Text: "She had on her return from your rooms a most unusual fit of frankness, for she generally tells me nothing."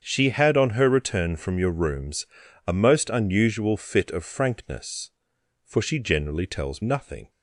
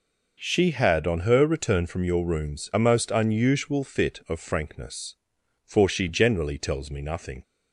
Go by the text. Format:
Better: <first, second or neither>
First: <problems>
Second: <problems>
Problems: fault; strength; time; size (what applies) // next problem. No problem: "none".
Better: second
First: starts louder than the rest; strong; until 1.0 s; 7.5 dB // pauses between "rooms" and "a"; at 2.2 s; 0.40 s long // skips "me"; at 6.8 s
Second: none